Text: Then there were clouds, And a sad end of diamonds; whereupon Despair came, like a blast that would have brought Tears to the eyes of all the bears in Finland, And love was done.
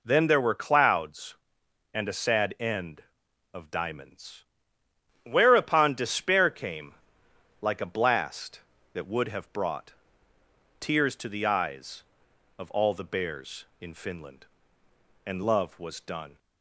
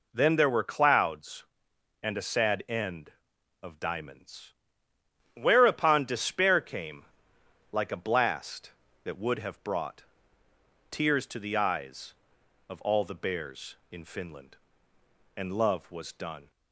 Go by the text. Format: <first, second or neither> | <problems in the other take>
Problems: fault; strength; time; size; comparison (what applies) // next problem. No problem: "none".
neither | pauses between "brought" and "Tears"; noticeable; the same in both